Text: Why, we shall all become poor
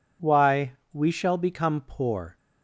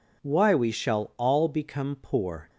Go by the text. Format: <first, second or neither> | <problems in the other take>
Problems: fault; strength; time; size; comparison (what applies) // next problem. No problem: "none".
second | skips "all"; at 1.3 s